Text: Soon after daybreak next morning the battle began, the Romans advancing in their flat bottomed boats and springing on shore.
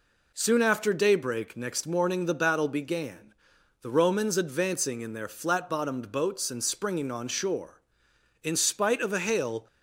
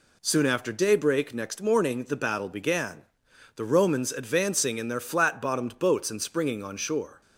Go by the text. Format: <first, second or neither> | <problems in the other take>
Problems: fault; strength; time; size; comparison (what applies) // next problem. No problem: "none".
second | goes on to say "In spite of a hail"; noticeable; from 8.4 s on; 1.2 s long